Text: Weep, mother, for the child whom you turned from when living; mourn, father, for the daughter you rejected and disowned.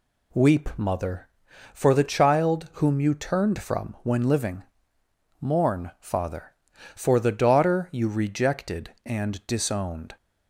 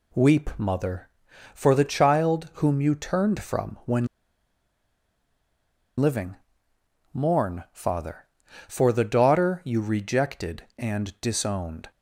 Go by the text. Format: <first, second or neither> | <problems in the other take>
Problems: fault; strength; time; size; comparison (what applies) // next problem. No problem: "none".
first | pauses between "when" and "living"; strong; at 4.0 s; 1.9 s long